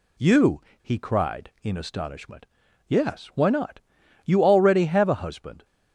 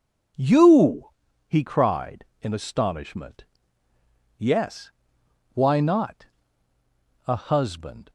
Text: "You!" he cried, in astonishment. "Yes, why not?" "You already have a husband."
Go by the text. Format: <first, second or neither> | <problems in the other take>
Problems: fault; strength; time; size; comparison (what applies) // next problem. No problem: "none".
first | skips "You already have"; at 6.7 s